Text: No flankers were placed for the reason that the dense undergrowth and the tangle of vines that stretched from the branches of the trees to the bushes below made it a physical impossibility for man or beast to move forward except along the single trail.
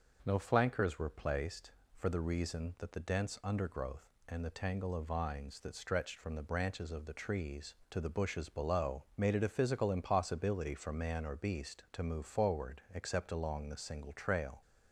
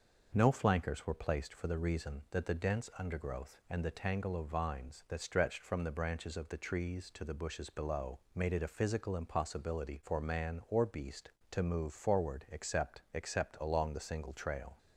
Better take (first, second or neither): first